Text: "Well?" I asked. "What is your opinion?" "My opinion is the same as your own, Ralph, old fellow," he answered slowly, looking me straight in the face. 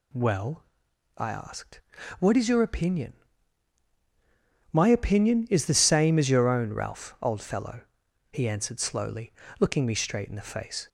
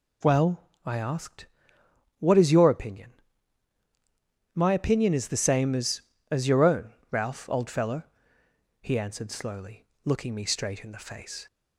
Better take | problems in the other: first | says "as" twice; at 6.2 s

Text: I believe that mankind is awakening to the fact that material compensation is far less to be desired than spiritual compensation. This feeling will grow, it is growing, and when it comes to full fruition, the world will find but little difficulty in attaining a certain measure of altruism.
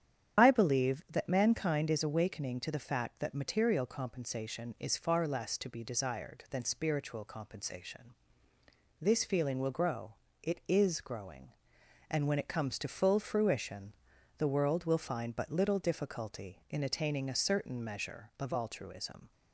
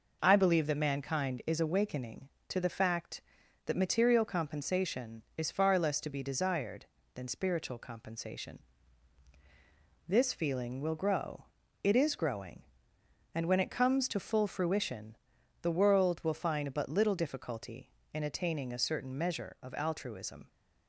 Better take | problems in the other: second | loses the start of "I"; at 0.3 s; 50 ms // starts louder than the rest; strong; until 1.4 s; 9 dB

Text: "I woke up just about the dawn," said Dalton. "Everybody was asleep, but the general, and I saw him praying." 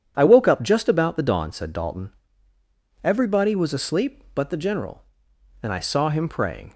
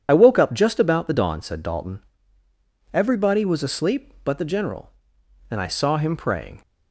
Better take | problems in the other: first | loses the start of "I"; at 0.0 s; 30 ms

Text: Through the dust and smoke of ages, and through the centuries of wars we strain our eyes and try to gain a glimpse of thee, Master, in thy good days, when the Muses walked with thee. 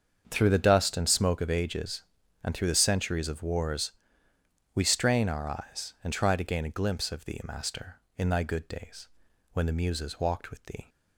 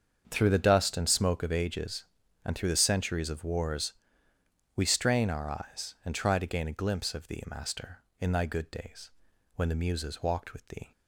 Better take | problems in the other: neither | starts louder than the rest; the same in both // pauses between "wars" and "we"; noticeable; the same in both

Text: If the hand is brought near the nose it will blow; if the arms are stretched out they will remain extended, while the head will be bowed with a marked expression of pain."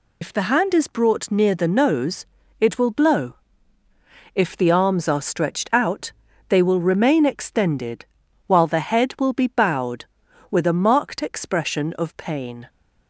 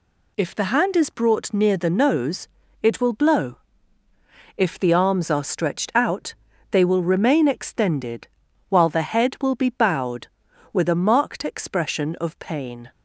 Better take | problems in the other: second | loses the start of "If"; at 0.2 s; 70 ms // pauses between "nose" and "it"; slight; at 2.2 s; 0.36 s long; slight in the second // pauses between "out" and "they"; slight; at 6.1 s; 0.36 s long; slight in the second

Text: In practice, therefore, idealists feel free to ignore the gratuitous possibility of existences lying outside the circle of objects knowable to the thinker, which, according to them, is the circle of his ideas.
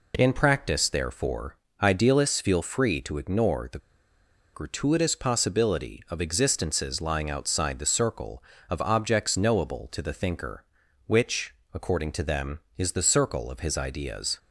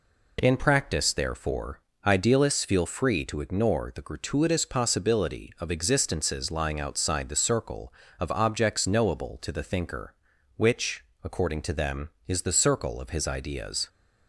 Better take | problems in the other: second | pauses between "the" and "gratuitous"; noticeable; at 3.7 s; 0.75 s long

